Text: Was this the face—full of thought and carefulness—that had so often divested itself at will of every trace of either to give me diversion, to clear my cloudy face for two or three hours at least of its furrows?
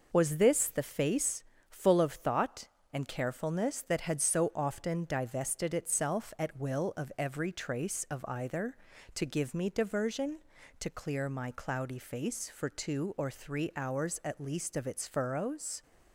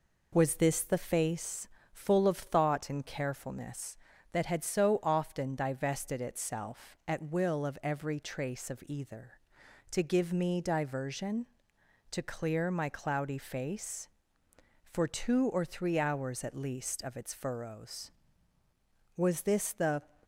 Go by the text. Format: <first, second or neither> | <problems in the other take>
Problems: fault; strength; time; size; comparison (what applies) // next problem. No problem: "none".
first | goes on to say "Was this the"; noticeable; from 19.1 s on; 0.86 s long